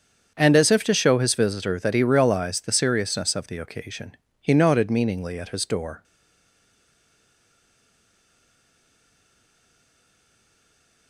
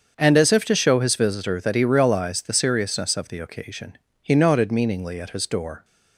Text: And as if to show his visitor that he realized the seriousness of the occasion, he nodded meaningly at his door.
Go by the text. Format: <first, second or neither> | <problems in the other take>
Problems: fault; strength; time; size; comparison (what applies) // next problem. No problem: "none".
second | starts louder than the rest; strong; until 1.3 s; 7 dB; strong in the second // stays silent after the last word; strong; from 6.0 s on; 5.0 s long